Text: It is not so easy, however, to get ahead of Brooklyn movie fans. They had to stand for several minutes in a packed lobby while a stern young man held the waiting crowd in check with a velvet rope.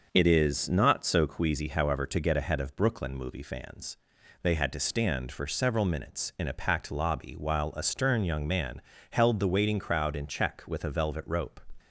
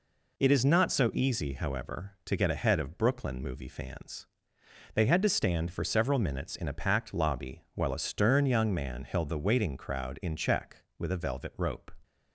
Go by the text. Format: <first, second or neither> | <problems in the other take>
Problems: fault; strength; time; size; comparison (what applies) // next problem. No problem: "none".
second | starts louder than the rest; noticeable; until 1.1 s; 6 dB // says "queasy" for "easy"; at 1.2 s // pauses between "man" and "held"; slight; at 8.8 s; 0.30 s long